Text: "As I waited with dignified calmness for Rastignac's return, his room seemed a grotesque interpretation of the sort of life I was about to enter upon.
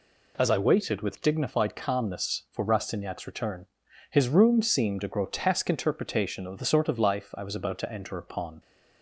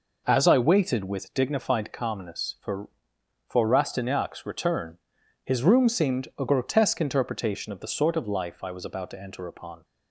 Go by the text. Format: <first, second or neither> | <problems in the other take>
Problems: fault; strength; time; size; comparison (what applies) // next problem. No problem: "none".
first | says "for" twice; at 3.4 s